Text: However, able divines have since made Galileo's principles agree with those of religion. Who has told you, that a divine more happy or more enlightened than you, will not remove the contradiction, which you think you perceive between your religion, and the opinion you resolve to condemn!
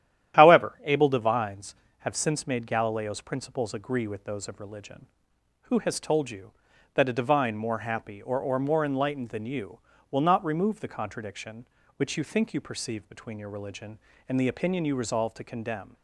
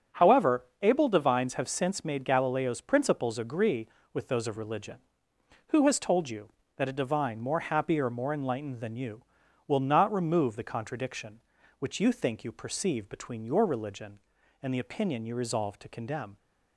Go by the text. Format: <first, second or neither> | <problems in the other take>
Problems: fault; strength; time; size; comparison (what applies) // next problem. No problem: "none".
second | starts louder than the rest; strong; until 1.3 s; 11 dB; also in the second // says "or" twice; at 8.4 s